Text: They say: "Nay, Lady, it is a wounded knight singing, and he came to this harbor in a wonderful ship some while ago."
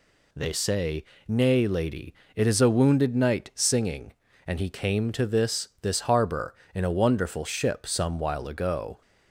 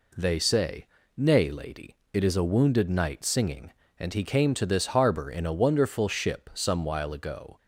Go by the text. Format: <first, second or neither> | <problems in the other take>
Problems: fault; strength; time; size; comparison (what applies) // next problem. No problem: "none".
second | says "this" twice; at 5.8 s